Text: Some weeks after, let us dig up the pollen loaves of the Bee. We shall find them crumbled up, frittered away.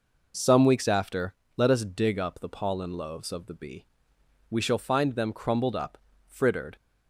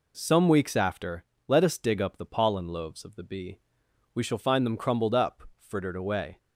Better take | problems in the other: second | stops before "away"; at 6.7 s

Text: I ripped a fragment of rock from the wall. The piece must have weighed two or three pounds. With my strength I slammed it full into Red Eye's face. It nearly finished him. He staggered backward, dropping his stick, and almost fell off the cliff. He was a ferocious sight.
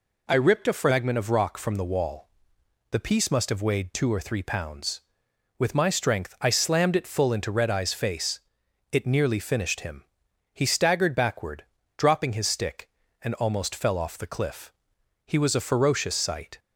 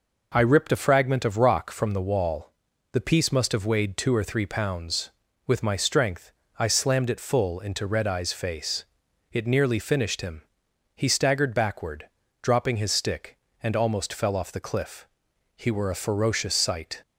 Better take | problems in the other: first | pauses between "strength" and "I"; slight; at 6.3 s; 0.26 s long // says "were" for "was"; at 15.6 s

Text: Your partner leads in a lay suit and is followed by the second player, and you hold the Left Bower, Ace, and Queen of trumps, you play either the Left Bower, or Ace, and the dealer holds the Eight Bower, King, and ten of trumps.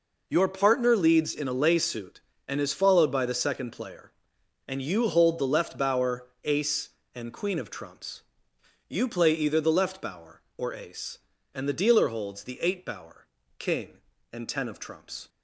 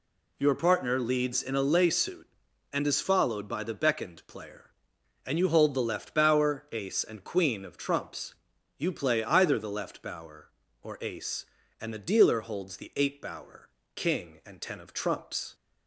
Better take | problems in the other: first | says "beckoned" for "second"; at 3.7 s

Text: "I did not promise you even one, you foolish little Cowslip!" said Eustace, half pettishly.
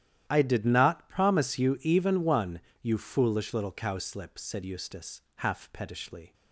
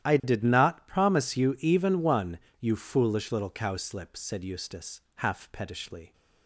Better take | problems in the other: neither | starts louder than the rest; strong; the same in both

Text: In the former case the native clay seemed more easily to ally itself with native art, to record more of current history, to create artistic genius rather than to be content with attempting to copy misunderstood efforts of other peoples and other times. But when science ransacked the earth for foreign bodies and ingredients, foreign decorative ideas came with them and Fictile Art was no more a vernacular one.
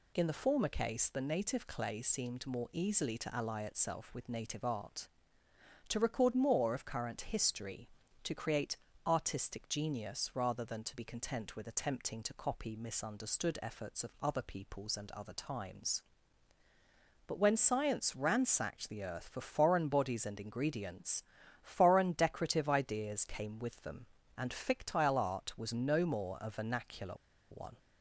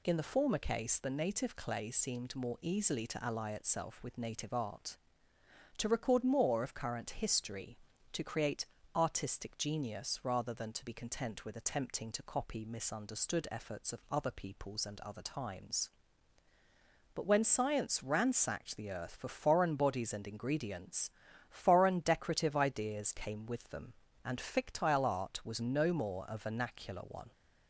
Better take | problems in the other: second | pauses between "create" and "artistic"; slight; at 8.7 s; 0.30 s long; slight in the second // pauses between "vernacular" and "one"; at 27.1 s; 0.36 s long

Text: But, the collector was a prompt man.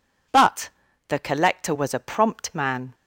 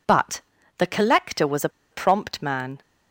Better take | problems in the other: first | pauses between "a" and "prompt"; slight; at 1.6 s; 0.23 s long

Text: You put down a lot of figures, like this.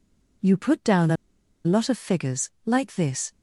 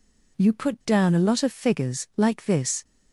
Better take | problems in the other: second | pauses between "a" and "lot"; noticeable; at 1.1 s; 0.50 s long

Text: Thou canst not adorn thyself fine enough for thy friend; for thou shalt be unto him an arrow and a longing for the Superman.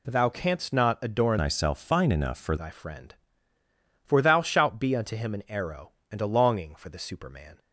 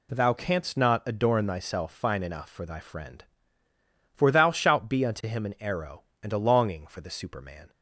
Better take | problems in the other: second | changes voice from "thyself" to "for"; from 1.3 to 2.5 s; 1.2 s long

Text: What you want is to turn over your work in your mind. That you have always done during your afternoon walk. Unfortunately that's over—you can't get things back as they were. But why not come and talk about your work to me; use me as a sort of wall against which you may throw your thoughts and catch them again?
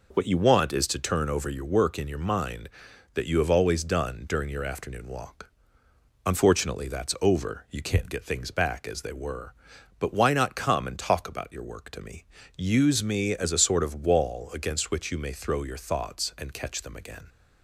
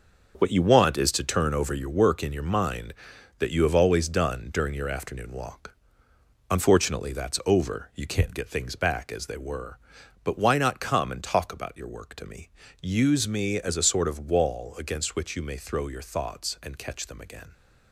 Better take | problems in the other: first | gets quieter; strong; throughout; 8.5 dB

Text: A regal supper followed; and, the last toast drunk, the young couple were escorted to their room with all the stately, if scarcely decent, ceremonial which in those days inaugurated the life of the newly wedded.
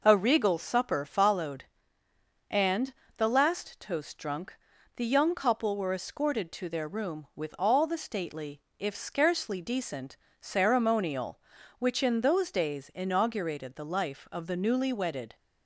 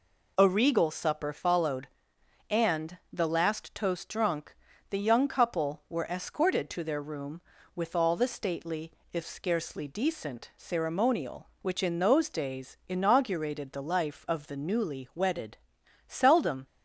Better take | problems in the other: first | goes on to say "Seldom"; from 16.0 s on; 0.60 s long

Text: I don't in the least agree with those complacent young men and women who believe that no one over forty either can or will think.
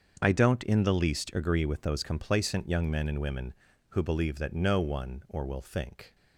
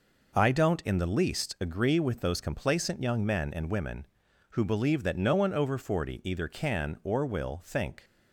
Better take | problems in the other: second | starts louder than the rest; until 1.2 s; 7 dB // skips "over forty either can"; at 5.2 s

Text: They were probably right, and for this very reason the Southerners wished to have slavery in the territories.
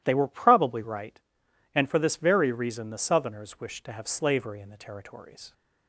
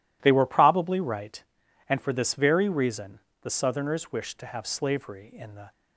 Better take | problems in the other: first | pauses between "reason" and "the"; slight; at 3.1 s; 0.22 s long // stops before "territories"; at 5.7 s

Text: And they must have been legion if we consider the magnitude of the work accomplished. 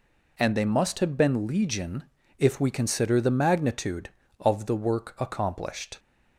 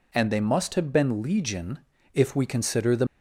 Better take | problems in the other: first | pauses between "legion" and "if"; slight; at 1.8 s; 0.34 s long; slight in the first // stops before "magnitude of the work accomplished"; at 3.0 s

